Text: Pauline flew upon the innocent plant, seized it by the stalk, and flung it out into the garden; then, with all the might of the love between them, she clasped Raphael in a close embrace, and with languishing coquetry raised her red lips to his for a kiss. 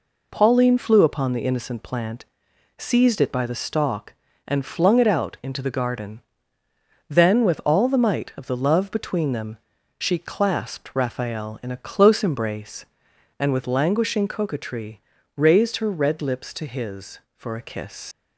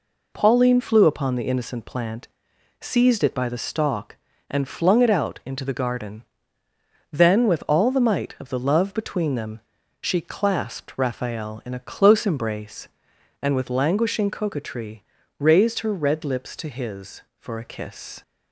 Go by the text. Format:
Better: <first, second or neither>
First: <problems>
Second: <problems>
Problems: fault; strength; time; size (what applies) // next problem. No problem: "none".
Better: second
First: pauses between "coquetry" and "raised"; slight; at 14.9 s; 0.36 s long // leaves "kiss" unfinished; at 18.1 s; 80 ms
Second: pauses between "coquetry" and "raised"; slight; at 15.0 s; 0.36 s long